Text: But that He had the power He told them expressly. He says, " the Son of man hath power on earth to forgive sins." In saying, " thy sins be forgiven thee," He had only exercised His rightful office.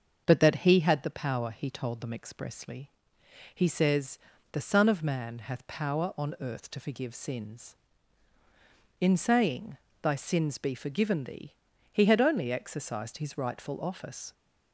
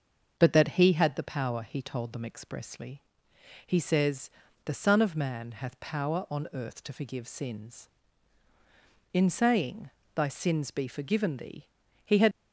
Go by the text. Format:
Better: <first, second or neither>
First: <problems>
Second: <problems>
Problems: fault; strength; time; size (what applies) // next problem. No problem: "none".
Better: first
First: starts louder than the rest; until 1.2 s; 7 dB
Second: starts louder than the rest; until 1.4 s; 7 dB // stops before "only exercised His rightful office"; at 12.3 s